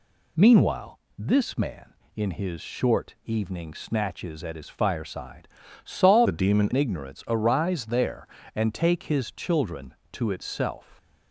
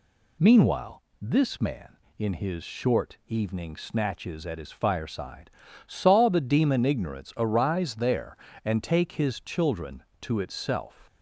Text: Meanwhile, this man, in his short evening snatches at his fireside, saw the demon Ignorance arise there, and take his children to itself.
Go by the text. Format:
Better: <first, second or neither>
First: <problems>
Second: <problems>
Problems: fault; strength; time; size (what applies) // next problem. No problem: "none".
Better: second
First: changes voice from "the" to "demon"; from 6.2 to 6.7 s; 0.5 s long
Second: none